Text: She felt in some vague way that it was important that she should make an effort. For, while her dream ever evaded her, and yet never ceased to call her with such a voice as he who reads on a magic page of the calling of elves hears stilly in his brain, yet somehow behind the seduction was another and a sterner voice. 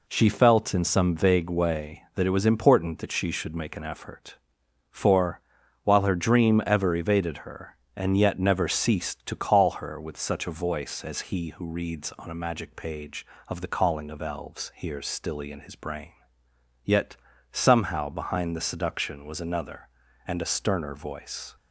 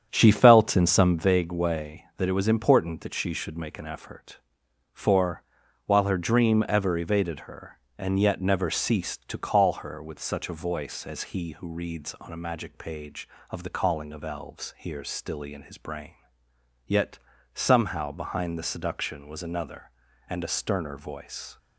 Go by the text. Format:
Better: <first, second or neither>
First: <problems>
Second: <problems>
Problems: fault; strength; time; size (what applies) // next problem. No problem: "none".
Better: first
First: pauses between "yet" and "somehow"; slight; at 17.1 s; 0.36 s long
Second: starts louder than the rest; strong; until 1.3 s; 8.5 dB // pauses between "yet" and "somehow"; slight; at 17.1 s; 0.36 s long